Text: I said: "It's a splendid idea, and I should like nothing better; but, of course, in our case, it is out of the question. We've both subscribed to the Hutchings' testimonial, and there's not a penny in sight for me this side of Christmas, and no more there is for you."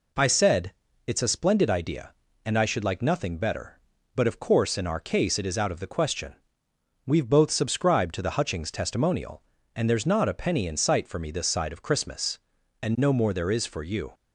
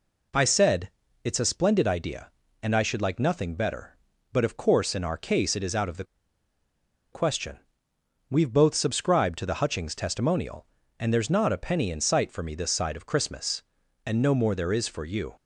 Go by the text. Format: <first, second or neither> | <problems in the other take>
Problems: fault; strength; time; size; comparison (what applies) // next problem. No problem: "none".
first | pauses between "the" and "question"; at 6.0 s; 1.0 s long